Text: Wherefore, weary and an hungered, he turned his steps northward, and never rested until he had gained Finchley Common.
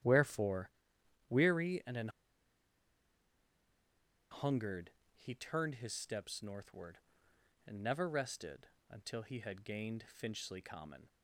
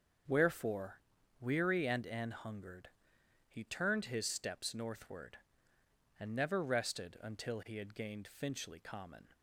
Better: second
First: starts louder than the rest; strong; until 1.6 s; 11.5 dB // pauses between "an" and "hungered"; strong; at 2.0 s; 2.2 s long // pauses between "rested" and "until"; slight; at 8.6 s; 0.22 s long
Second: starts louder than the rest; until 1.6 s; 6.5 dB

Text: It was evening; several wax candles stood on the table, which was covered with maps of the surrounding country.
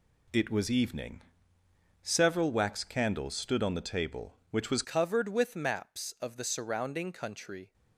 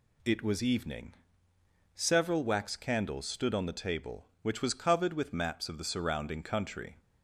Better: second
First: changes voice at "covered"; from 4.8 s on; 2.9 s long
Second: none

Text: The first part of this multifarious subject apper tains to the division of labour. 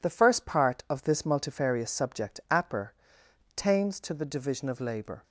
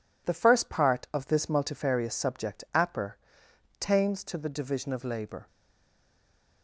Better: first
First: pauses between "apper" and "tains"; noticeable; at 2.9 s; 0.66 s long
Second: pauses between "apper" and "tains"; noticeable; at 3.1 s; 0.66 s long // stays silent after the last word; noticeable; from 5.4 s on; 1.2 s long

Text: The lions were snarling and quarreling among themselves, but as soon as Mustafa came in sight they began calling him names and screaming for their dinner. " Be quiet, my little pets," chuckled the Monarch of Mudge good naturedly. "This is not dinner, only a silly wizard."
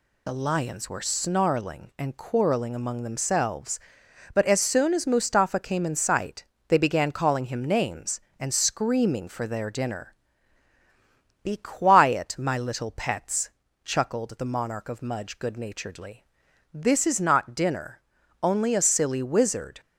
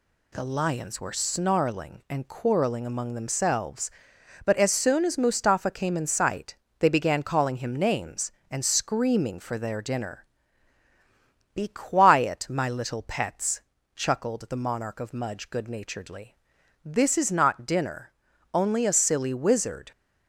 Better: second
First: loses the start of "The"; at 0.2 s; 45 ms // pauses between "sight" and "they"; slight; at 6.4 s; 0.24 s long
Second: pauses between "sight" and "they"; slight; at 6.5 s; 0.24 s long

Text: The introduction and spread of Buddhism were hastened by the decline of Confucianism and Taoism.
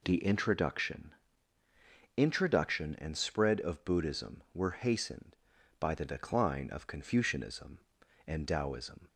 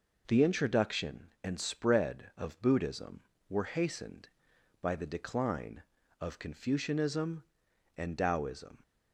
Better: second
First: says "introduction" twice; at 2.1 s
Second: none

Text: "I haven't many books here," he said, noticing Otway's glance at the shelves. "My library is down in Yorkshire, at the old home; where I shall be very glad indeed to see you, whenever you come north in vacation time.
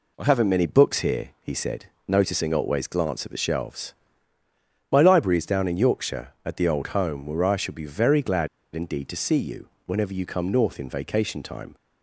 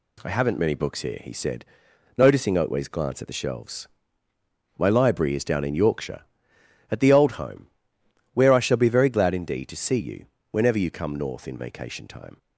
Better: second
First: pauses between "glad" and "indeed"; slight; at 8.4 s; 0.25 s long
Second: none

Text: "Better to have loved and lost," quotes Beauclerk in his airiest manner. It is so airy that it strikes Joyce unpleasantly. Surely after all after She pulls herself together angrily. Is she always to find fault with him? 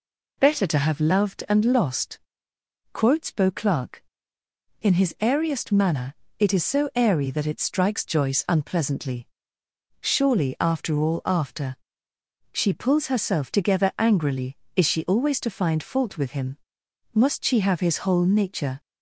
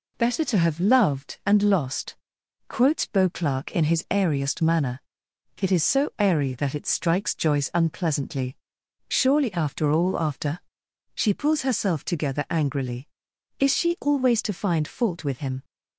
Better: second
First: pauses between "after" and "She"; noticeable; at 11.7 s; 0.76 s long // goes on to say "Must she have his whole nature"; from 17.1 s on; 1.6 s long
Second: pauses between "after" and "She"; noticeable; at 10.5 s; 0.56 s long

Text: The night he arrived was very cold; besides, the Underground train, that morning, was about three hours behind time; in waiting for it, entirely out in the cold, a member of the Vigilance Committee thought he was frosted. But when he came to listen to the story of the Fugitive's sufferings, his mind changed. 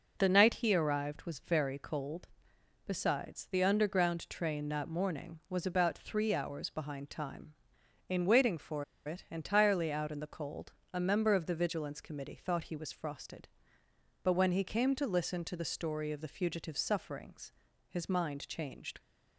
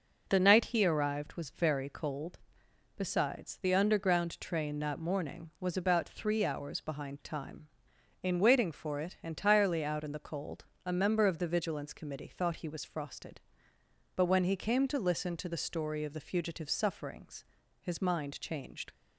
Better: second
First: pauses between "for" and "it"; slight; at 8.8 s; 0.23 s long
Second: none

